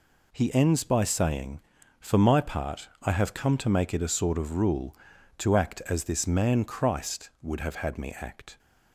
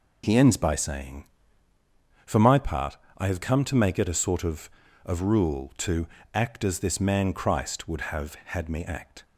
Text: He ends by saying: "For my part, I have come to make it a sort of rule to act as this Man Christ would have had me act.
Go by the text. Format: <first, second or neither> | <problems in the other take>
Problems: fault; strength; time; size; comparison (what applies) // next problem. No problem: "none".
first | says "of" twice; at 5.0 s // pauses between "to" and "act"; slight; at 6.0 s; 0.26 s long